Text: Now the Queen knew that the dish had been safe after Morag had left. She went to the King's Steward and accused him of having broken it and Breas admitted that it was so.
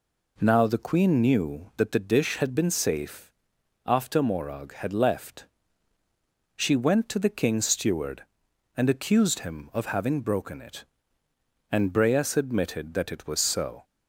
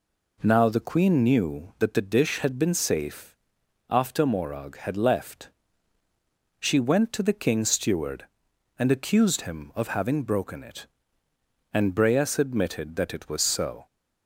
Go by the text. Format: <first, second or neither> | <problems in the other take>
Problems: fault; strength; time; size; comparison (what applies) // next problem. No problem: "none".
neither | pauses between "safe" and "after"; noticeable; the same in both